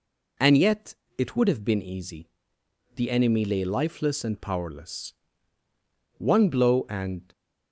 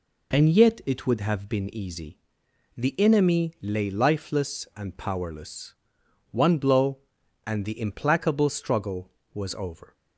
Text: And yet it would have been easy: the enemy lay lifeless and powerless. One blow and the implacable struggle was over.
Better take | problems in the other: second | pauses between "yet" and "it"; slight; at 0.9 s; 0.22 s long // stops before "the implacable struggle was over"; at 7.3 s

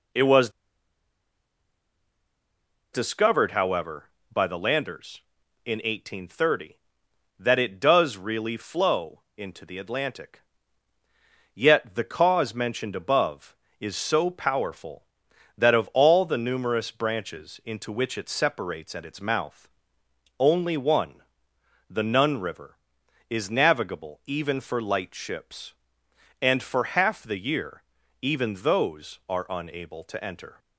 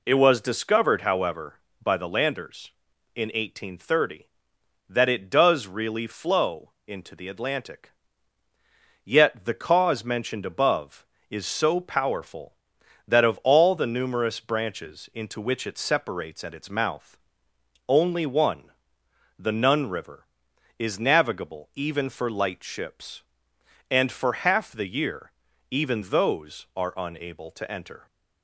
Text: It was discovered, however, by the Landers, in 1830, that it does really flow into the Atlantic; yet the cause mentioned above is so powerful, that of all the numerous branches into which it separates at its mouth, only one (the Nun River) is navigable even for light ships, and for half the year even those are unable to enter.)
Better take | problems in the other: second | pauses between "was" and "discovered"; strong; at 0.4 s; 2.4 s long // pauses between "flow" and "into"; slight; at 9.2 s; 0.18 s long; slight in the second // pauses between "year" and "even"; at 27.8 s; 0.40 s long; also in the second

